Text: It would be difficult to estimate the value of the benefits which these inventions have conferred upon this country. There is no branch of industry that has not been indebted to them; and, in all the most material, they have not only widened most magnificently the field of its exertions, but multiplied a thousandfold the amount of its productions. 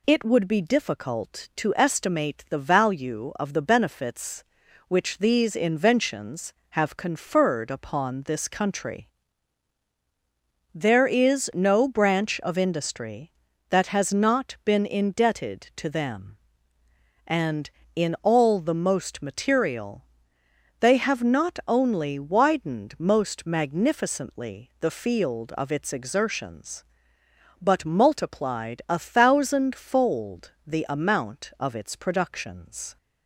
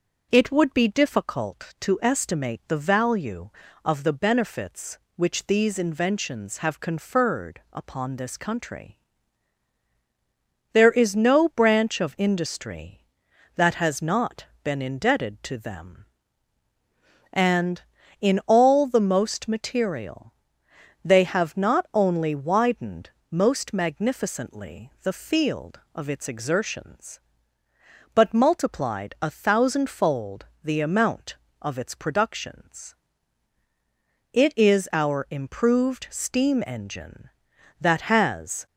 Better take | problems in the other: first | pauses between "not" and "been"; slight; at 14.4 s; 0.18 s long // pauses between "widened" and "most"; slight; at 23.1 s; 0.20 s long // pauses between "thousandfold" and "the"; slight; at 30.4 s; 0.18 s long; slight in the first // goes on to say "It is our improved steam engine that has"; strong; from 34.3 s on; 4.3 s long

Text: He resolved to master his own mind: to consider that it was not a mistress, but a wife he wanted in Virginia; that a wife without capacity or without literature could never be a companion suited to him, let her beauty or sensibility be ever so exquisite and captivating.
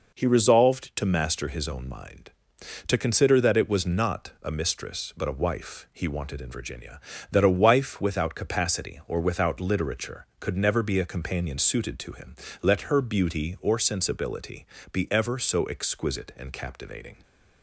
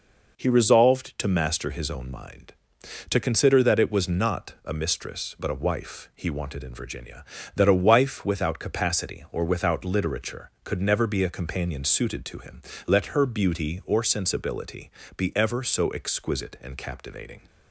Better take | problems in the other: neither | pauses between "sensibility" and "be"; slight; the same in both

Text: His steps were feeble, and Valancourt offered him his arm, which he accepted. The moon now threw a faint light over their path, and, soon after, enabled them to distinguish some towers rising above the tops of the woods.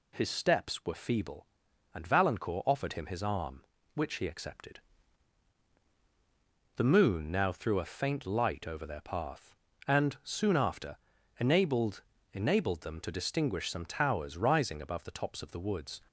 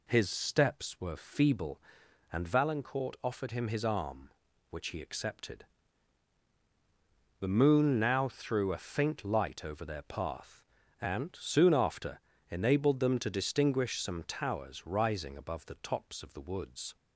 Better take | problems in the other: second | says "enabled" twice; at 12.3 s

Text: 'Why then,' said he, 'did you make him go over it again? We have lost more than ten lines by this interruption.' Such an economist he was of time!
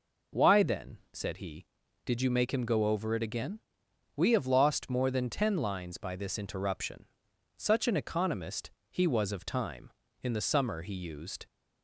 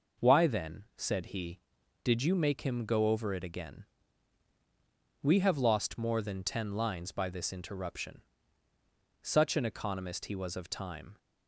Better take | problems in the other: second | pauses between "economist" and "he"; slight; at 8.7 s; 0.18 s long // goes on to say "In the summer he used"; noticeable; from 10.2 s on; 1.2 s long

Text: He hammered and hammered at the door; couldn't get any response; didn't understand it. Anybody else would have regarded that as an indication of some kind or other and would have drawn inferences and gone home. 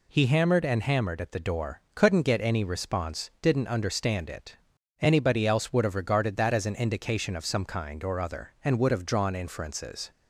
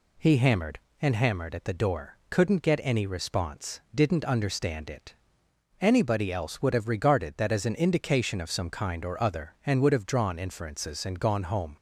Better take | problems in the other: second | stops before "and gone home"; at 10.1 s

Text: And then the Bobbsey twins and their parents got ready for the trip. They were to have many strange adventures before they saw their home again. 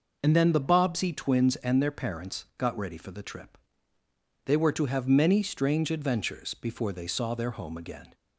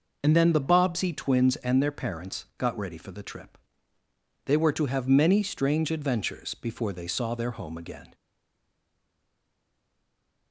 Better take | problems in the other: first | stays silent after the last word; from 8.1 s on; 2.4 s long

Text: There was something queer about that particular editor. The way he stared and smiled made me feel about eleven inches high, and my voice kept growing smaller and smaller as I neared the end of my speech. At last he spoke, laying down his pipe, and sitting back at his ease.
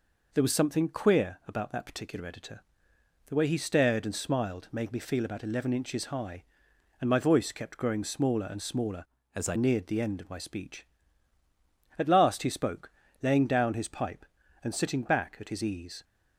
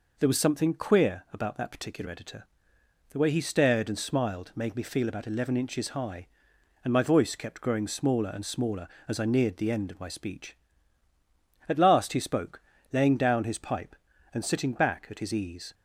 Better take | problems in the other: second | changes voice from "as" to "I"; from 9.3 to 9.5 s; 0.2 s long

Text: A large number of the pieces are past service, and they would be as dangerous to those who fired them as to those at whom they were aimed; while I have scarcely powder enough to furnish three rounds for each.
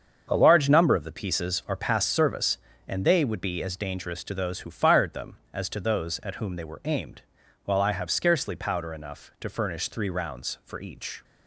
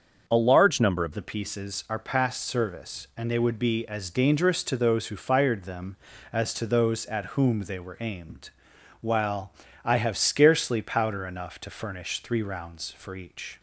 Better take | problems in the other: first | starts louder than the rest; until 1.3 s; 6.5 dB; also in the first // changes voice at "the"; from 1.1 s on; 12.4 s long // pauses between "while" and "I"; slight; at 9.5 s; 0.34 s long

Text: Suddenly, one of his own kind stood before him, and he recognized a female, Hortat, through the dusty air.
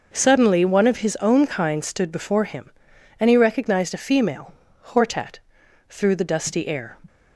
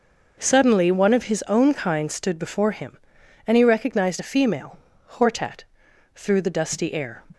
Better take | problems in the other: neither | none

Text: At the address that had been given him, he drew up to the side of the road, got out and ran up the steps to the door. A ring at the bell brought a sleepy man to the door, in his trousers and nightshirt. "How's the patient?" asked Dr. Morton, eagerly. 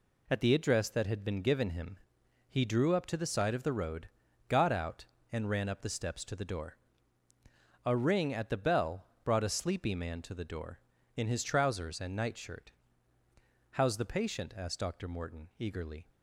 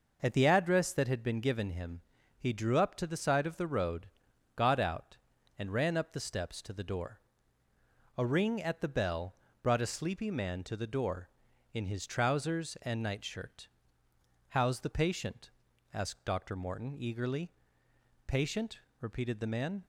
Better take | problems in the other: first | pauses between "bell" and "brought"; slight; at 9.3 s; 0.28 s long; slight in the first // goes on to say "Patient repeated the man"; from 18.2 s on; 1.5 s long

